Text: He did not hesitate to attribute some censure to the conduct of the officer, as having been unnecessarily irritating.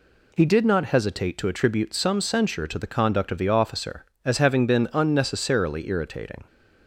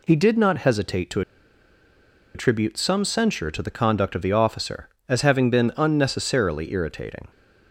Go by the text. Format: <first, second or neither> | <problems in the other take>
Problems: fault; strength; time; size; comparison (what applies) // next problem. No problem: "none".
first | pauses between "to" and "attribute"; at 1.2 s; 1.1 s long